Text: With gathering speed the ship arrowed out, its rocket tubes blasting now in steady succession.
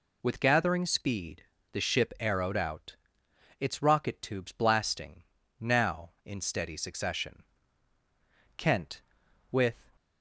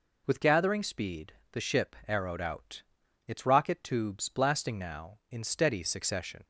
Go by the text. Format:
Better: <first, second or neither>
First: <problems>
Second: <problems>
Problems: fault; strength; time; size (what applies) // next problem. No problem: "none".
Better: second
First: pauses between "speed" and "the"; slight; at 1.4 s; 0.30 s long // pauses between "blasting" and "now"; at 5.2 s; 0.38 s long // goes on to say "Kent with"; noticeable; from 8.5 s on; 1.2 s long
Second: pauses between "speed" and "the"; slight; at 1.3 s; 0.18 s long